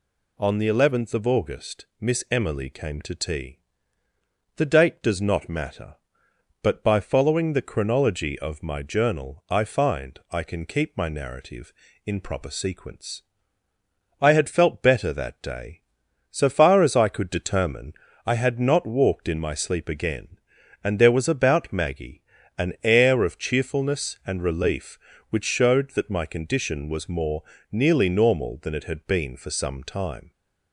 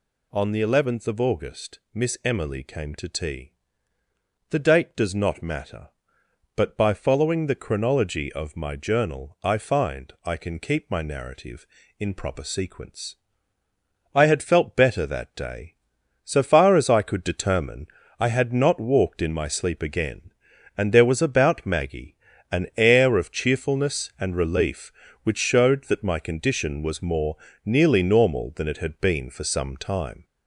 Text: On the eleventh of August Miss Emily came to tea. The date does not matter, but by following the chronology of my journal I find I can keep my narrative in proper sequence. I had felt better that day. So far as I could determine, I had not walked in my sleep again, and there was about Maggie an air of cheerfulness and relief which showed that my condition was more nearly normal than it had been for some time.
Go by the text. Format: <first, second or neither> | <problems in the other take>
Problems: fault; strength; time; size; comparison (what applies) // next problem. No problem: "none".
first | gets louder; noticeable; throughout; 4.5 dB // pauses between "Maggie" and "an"; at 22.1 s; 0.38 s long; also in the first // pauses between "more" and "nearly"; slight; at 27.3 s; 0.28 s long; slight in the first